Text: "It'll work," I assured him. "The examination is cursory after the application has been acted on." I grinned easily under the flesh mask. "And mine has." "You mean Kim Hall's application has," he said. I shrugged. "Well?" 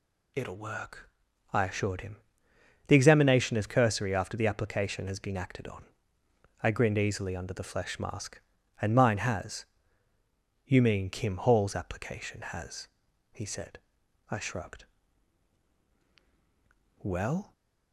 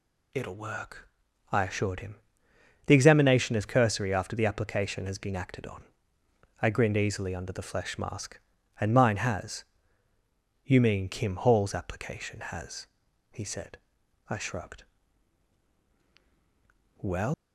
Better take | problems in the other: first | leaves "Well" unfinished; at 17.3 s; 170 ms

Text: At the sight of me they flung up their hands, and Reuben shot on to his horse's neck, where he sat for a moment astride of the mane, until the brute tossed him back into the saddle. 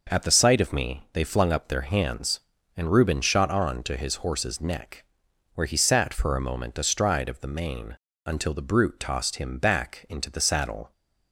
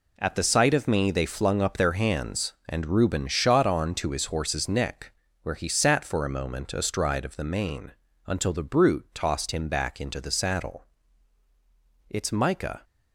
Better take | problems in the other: first | goes on to say "It's Micah"; noticeable; from 12.0 s on; 0.74 s long

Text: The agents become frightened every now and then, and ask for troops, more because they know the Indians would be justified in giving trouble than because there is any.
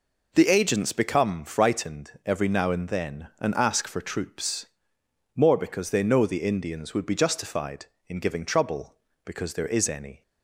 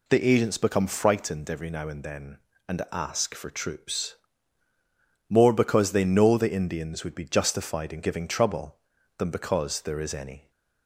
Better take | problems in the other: second | skips "than"; at 9.1 s

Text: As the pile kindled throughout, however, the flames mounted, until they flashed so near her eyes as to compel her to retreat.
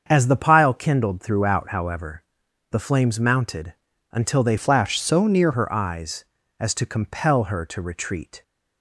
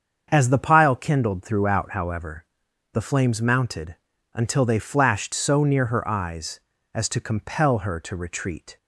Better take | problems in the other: second | starts louder than the rest; until 1.0 s; 7 dB; also in the second // changes voice from "flashed" to "near"; from 4.5 to 5.5 s; 1.0 s long

